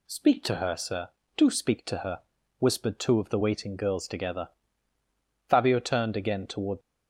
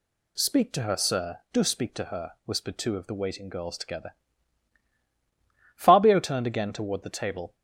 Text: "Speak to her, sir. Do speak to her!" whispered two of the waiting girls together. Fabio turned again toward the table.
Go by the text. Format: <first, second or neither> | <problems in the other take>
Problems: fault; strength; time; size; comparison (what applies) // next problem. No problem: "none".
second | stops before "the table"; at 6.8 s